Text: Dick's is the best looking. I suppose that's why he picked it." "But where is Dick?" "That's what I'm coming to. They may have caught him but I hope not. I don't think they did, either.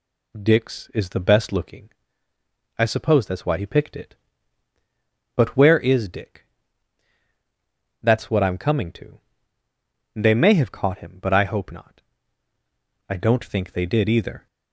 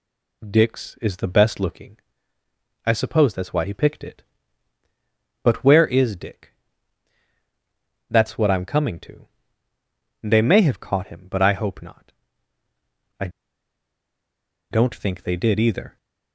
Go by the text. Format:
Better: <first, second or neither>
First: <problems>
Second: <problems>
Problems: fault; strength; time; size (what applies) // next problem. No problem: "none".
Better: first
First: none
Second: pauses between "I" and "don't"; strong; at 13.2 s; 1.4 s long